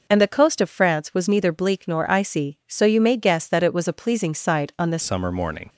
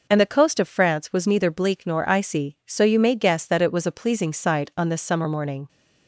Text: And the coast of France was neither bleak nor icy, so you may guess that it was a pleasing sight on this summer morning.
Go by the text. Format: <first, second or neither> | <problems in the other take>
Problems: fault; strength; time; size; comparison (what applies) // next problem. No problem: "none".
second | changes voice at "summer"; from 5.0 s on; 0.6 s long